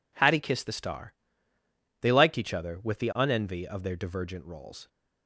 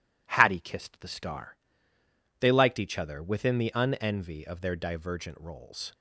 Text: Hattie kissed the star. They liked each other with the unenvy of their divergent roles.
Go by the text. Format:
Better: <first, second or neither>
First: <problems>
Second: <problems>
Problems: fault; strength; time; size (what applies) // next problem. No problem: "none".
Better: first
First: none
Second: says "within" for "with"; at 3.2 s